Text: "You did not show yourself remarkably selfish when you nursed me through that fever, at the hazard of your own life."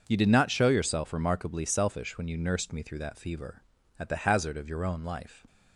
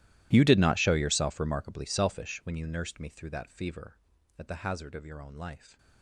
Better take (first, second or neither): first